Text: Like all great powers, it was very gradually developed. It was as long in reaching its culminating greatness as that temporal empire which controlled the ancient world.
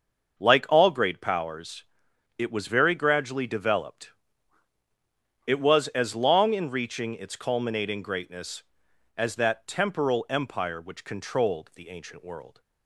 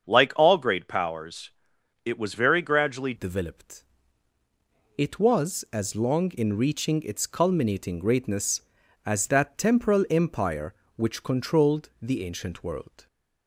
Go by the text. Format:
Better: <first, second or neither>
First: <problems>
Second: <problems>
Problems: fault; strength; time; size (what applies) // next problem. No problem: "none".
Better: first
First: starts louder than the rest; until 1.4 s; 6.5 dB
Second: starts louder than the rest; strong; until 1.1 s; 7 dB // changes voice at "developed"; from 3.1 s on; 9.9 s long